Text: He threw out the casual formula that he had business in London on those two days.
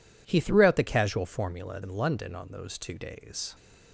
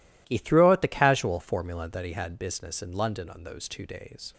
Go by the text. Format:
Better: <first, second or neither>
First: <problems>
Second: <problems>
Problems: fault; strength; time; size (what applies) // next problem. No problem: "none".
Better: second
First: skips "that he had business"; at 1.8 s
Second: none